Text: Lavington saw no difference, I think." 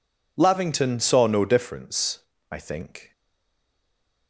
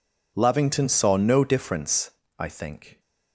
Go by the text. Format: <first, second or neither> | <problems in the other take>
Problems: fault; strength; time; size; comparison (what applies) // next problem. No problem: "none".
second | stays silent after the last word; noticeable; from 3.1 s on; 1.1 s long